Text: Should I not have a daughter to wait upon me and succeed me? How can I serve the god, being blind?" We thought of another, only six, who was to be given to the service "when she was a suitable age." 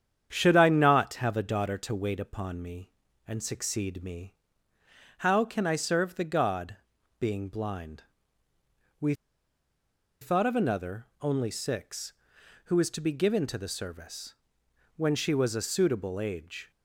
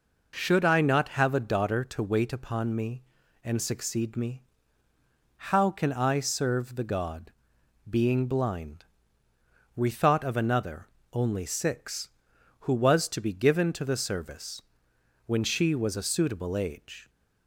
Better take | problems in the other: second | starts louder than the rest; strong; until 1.3 s; 8.5 dB // pauses between "We" and "thought"; at 9.1 s; 1.0 s long // pauses between "service" and "when"; noticeable; at 14.3 s; 0.64 s long; noticeable in the second

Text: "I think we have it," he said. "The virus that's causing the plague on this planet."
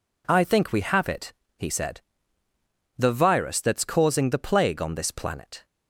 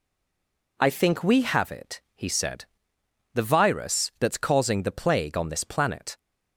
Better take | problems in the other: first | stays silent before the first word; slight; until 0.7 s; 0.7 s long

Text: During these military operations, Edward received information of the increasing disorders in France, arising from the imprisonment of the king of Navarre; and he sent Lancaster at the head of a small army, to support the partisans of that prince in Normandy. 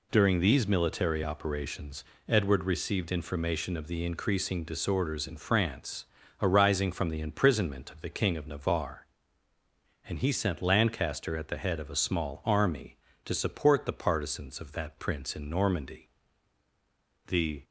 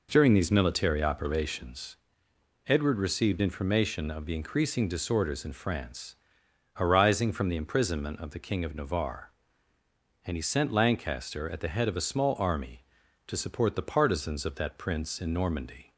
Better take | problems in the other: second | goes on to say "The"; slight; from 17.2 s on; 0.38 s long

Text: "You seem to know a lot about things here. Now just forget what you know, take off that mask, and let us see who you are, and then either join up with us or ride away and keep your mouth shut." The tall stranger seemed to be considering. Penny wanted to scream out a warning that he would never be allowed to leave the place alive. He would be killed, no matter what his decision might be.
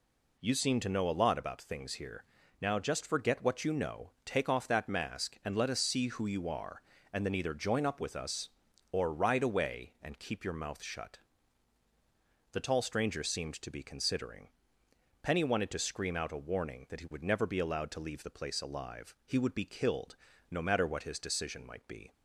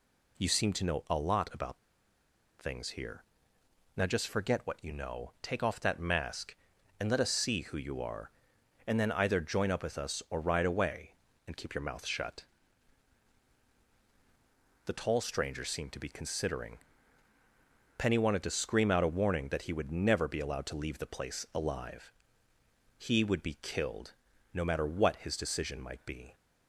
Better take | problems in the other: first | pauses between "about" and "things"; noticeable; at 1.7 s; 0.79 s long

